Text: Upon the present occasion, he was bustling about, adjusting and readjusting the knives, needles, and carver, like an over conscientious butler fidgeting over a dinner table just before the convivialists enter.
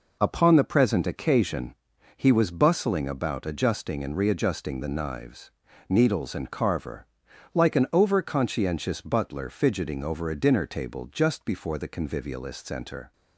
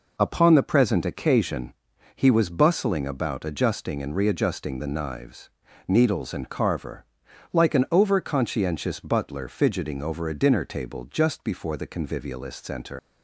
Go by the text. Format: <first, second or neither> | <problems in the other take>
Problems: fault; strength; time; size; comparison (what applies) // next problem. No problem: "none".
first | leaves "enter" unfinished; at 12.9 s; 120 ms